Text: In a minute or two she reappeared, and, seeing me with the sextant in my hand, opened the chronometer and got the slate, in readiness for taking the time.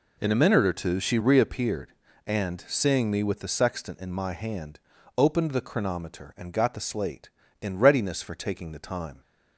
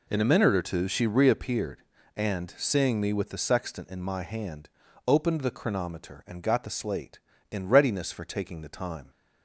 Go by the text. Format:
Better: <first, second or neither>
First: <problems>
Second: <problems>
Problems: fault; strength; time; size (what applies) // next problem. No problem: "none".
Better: neither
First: none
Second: none